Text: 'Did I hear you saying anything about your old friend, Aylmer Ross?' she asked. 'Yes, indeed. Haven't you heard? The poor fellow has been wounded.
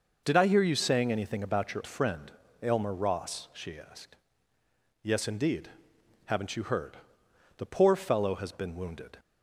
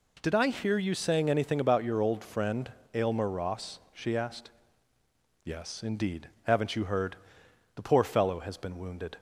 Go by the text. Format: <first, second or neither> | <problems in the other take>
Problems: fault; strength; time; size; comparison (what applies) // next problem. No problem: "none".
second | skips "old"; at 1.8 s